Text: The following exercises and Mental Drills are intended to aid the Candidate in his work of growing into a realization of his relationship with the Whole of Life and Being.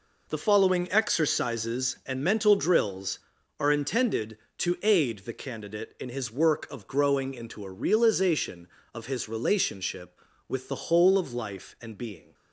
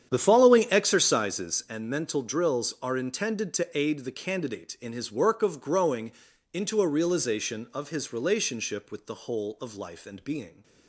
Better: first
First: none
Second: starts louder than the rest; strong; until 1.8 s; 9.5 dB // pauses between "growing" and "into"; at 6.1 s; 0.38 s long

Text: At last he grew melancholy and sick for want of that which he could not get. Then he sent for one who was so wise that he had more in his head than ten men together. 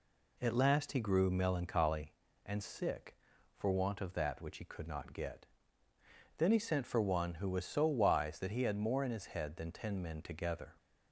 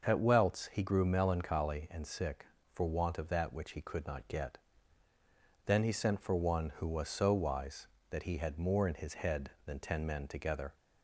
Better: first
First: none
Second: starts louder than the rest; noticeable; until 1.0 s; 6 dB // says "welts" for "last"; at 0.1 s

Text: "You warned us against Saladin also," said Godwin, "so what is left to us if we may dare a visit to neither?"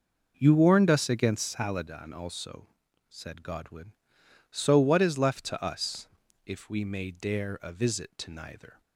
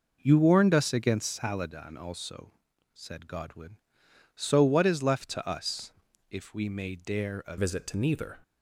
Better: first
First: pauses between "us" and "if"; slight; at 6.0 s; 0.36 s long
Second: pauses between "us" and "if"; slight; at 5.9 s; 0.36 s long // changes voice at "visit"; from 7.5 s on; 0.8 s long

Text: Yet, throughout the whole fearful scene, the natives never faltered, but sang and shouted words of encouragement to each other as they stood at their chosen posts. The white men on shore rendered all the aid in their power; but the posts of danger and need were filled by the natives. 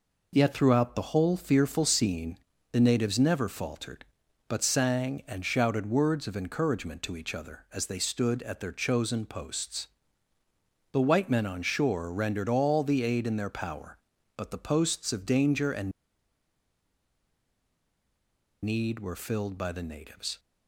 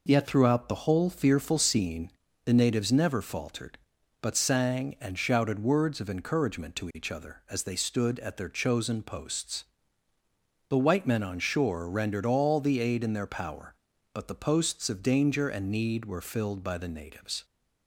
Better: second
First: pauses between "and" and "need"; strong; at 15.9 s; 2.7 s long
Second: none

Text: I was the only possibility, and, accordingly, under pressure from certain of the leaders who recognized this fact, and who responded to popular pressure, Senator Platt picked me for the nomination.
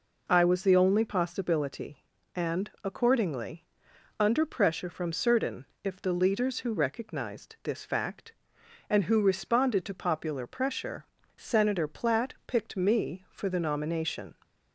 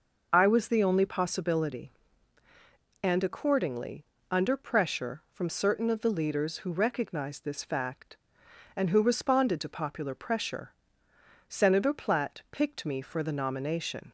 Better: second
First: says "if" for "of"; at 5.8 s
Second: none

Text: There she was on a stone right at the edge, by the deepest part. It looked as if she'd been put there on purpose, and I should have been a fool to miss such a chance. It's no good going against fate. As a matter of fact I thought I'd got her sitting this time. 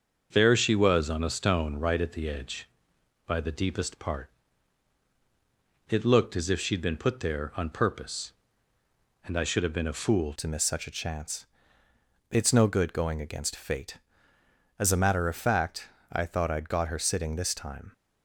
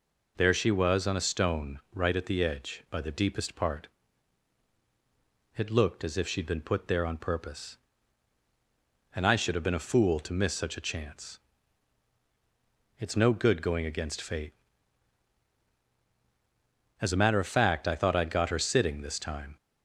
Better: second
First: starts louder than the rest; until 1.3 s; 6.5 dB // changes voice at "to"; from 10.3 s on; 7.6 s long // pauses between "fact" and "I"; slight; at 15.8 s; 0.24 s long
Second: none

